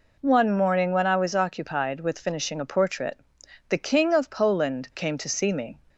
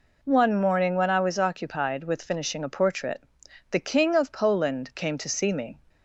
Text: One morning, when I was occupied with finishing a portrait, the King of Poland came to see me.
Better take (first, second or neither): neither